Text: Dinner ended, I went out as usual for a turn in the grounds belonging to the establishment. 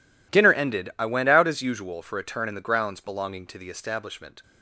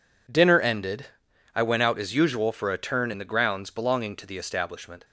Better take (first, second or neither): neither